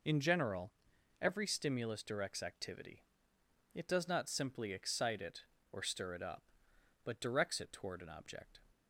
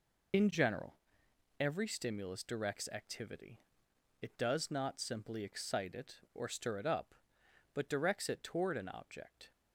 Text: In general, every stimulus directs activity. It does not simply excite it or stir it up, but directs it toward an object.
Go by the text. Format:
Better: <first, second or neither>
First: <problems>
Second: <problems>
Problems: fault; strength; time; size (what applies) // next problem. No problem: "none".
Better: first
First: none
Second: loses the start of "In"; at 0.3 s; 50 ms